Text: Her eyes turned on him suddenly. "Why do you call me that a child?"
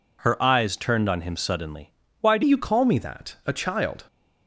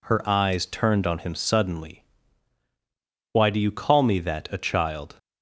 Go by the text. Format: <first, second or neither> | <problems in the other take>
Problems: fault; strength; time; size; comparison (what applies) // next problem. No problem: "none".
second | changes voice at "you"; from 2.4 s on; 1.6 s long